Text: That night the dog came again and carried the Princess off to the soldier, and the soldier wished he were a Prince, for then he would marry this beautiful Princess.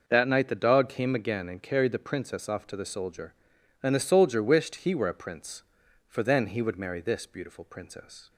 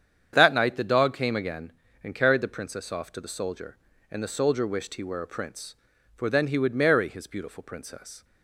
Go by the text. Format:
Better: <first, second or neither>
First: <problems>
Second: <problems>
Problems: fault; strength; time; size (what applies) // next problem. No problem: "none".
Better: first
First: none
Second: starts louder than the rest; strong; until 1.3 s; 8.5 dB // says "his" for "this"; at 7.0 s